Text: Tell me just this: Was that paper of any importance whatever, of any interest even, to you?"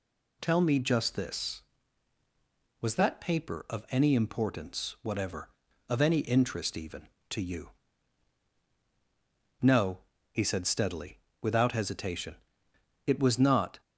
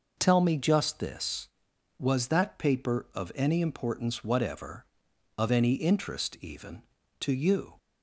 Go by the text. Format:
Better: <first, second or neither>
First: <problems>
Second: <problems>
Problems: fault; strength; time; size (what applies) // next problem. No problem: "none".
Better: second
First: goes on to say "No he said steadily without hesitation It was not"; strong; from 9.6 s on; 4.2 s long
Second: none